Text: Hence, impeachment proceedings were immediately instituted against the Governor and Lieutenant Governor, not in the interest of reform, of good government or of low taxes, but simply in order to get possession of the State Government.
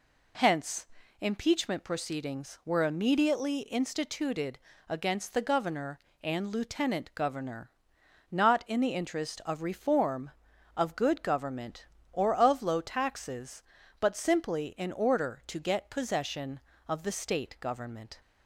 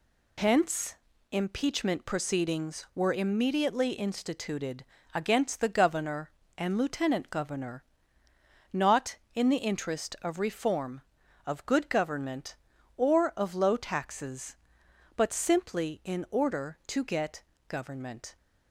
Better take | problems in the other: first | pauses between "instituted" and "against"; slight; at 4.8 s; 0.28 s long; slight in the first // skips "possession of the State"; at 17.5 s

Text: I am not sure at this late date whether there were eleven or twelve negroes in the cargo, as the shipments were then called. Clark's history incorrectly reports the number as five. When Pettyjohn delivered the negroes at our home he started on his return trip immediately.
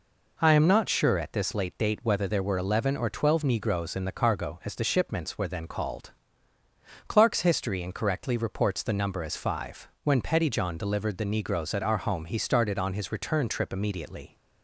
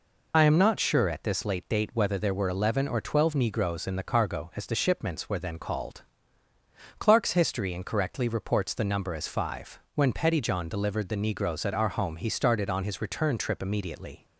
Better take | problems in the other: first | loses the start of "I"; at 0.3 s; 50 ms

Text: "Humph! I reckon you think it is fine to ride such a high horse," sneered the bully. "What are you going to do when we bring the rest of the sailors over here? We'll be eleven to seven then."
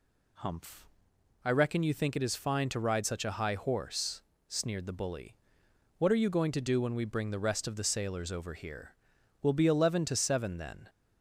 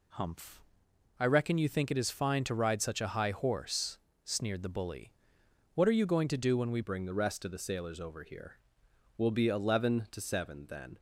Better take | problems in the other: first | changes voice at "bring"; from 6.8 s on; 4.1 s long

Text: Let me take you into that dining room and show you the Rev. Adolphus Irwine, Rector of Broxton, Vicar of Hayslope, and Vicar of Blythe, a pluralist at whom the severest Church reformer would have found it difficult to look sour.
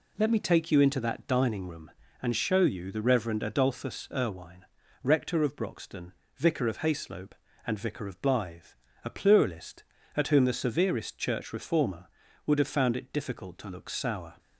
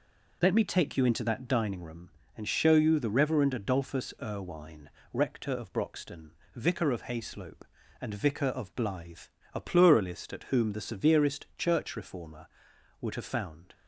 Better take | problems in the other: first | stops before "it difficult to look sour"; at 13.7 s

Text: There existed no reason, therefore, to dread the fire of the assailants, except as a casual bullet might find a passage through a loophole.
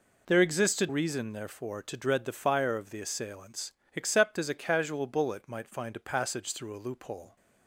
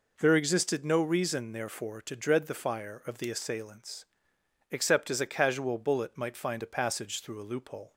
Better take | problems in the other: second | skips "no"; at 0.8 s

